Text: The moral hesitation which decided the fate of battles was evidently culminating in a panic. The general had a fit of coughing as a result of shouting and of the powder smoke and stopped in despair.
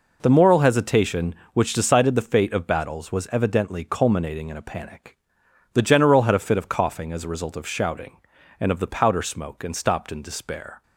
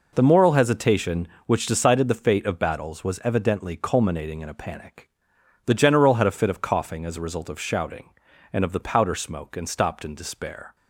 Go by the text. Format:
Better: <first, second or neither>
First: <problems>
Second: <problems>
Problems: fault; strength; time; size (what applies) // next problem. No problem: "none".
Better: neither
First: none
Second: none